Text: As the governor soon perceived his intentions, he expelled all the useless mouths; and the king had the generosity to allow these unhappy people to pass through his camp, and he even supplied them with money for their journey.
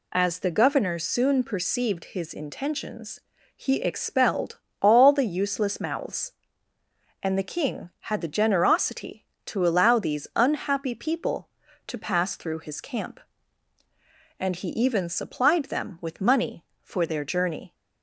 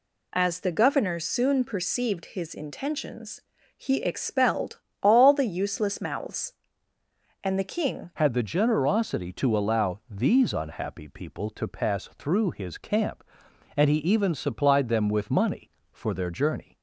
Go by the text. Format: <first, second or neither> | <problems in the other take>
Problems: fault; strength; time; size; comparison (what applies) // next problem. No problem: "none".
first | pauses between "expelled" and "all"; slight; at 4.7 s; 0.22 s long; slight in the first // changes voice at "had"; from 8.1 s on; 8.6 s long